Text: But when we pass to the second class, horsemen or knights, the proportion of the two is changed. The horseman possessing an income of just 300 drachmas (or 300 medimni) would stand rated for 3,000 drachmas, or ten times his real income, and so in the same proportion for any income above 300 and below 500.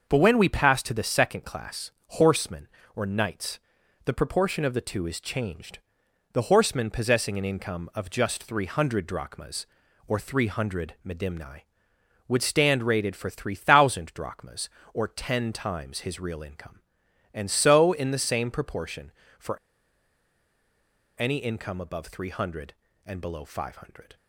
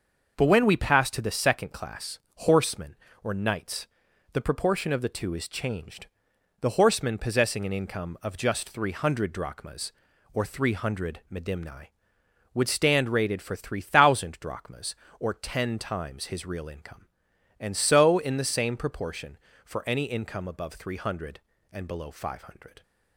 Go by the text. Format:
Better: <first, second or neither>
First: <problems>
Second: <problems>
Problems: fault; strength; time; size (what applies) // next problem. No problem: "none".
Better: second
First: starts louder than the rest; until 1.1 s; 6.5 dB // pauses between "for" and "any"; strong; at 19.5 s; 1.6 s long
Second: starts louder than the rest; until 1.3 s; 6.5 dB